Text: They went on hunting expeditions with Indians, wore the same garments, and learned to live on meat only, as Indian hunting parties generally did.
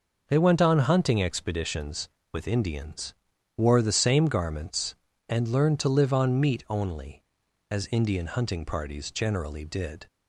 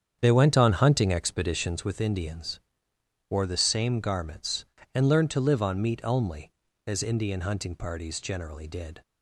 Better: first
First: none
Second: starts louder than the rest; strong; until 2.0 s; 8 dB

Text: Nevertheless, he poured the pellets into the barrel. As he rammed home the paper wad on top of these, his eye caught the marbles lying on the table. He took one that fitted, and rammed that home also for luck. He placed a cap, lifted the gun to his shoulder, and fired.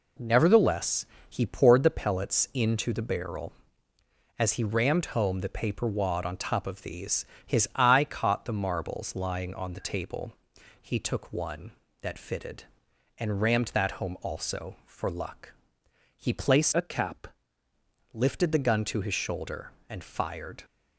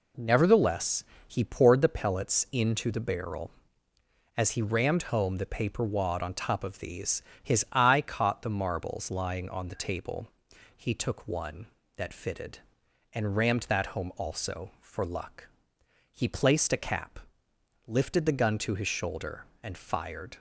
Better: second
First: changes voice from "a" to "cap"; from 16.7 to 17.2 s; 0.5 s long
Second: none

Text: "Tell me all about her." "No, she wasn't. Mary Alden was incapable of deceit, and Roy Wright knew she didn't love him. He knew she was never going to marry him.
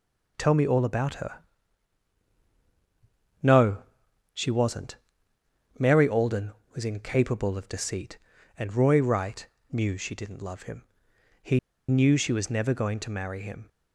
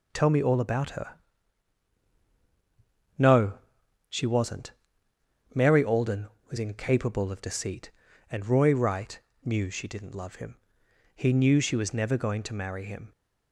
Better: second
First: pauses between "Wright" and "knew"; slight; at 9.4 s; 0.24 s long // pauses between "He" and "knew"; slight; at 11.5 s; 0.30 s long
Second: pauses between "Wright" and "knew"; slight; at 9.1 s; 0.24 s long

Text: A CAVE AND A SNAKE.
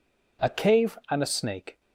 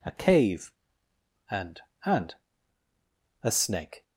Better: first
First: none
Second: says "AND" twice; at 2.0 s

